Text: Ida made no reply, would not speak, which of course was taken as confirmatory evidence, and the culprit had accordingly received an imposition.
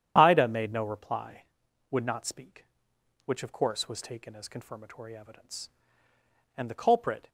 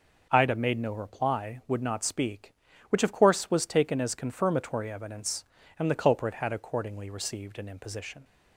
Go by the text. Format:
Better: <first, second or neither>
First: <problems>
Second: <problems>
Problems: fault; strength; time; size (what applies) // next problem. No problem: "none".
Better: second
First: starts louder than the rest; strong; until 1.1 s; 9.5 dB // stops before "had accordingly received an imposition"; at 7.2 s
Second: none